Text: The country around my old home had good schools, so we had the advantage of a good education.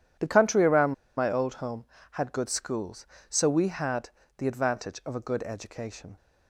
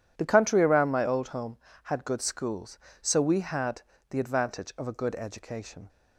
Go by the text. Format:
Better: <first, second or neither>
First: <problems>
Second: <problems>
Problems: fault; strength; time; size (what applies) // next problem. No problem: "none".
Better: second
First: pauses between "around" and "my"; slight; at 0.9 s; 0.23 s long // pauses between "had" and "the"; slight; at 4.0 s; 0.30 s long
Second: pauses between "had" and "the"; slight; at 3.8 s; 0.30 s long